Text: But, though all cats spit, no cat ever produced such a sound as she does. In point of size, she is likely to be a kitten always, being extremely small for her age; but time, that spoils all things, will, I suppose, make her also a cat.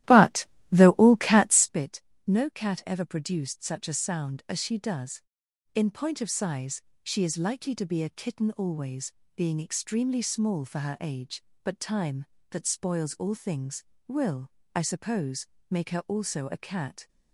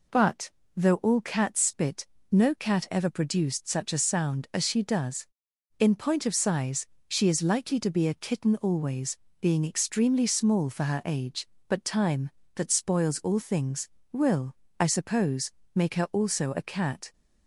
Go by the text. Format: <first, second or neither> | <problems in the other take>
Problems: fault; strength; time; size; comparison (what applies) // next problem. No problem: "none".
second | starts louder than the rest; strong; until 1.8 s; 14 dB